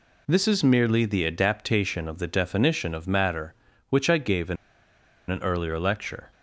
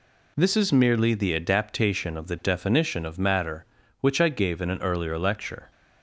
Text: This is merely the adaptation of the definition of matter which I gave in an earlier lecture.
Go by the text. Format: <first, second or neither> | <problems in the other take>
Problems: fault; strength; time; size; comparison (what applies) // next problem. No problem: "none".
second | pauses between "in" and "an"; noticeable; at 4.5 s; 0.74 s long